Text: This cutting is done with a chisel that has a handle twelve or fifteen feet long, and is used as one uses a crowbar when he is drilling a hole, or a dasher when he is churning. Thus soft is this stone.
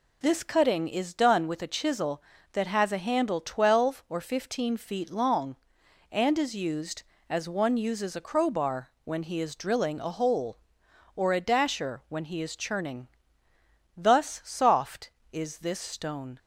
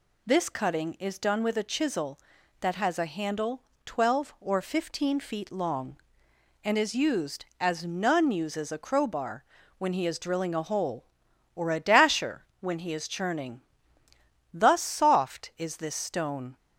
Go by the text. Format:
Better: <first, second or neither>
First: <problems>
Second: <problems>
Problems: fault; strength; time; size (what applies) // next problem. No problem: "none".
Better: first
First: none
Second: pauses between "handle" and "twelve"; slight; at 3.6 s; 0.22 s long // says "none" for "one"; at 7.8 s // pauses between "crowbar" and "when"; slight; at 9.4 s; 0.36 s long